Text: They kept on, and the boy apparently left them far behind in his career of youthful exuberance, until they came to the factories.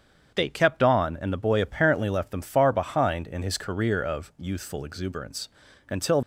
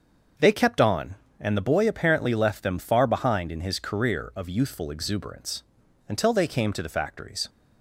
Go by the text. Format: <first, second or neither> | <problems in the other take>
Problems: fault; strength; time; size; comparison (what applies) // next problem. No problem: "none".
second | starts louder than the rest; strong; until 1.3 s; 7.5 dB; also in the second // stops before "they came to the factories"; at 6.2 s